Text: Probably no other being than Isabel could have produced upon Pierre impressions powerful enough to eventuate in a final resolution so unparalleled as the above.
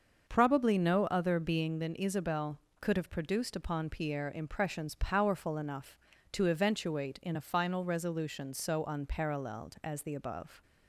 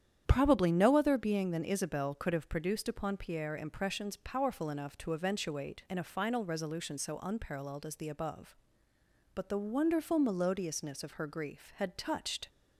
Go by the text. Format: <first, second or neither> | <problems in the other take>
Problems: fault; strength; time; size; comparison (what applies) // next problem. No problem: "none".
first | starts louder than the rest; strong; until 1.2 s; 9 dB; also in the first // goes on to say "But the wonderful melodiousness of her grief had touched"; strong; from 9.3 s on; 3.1 s long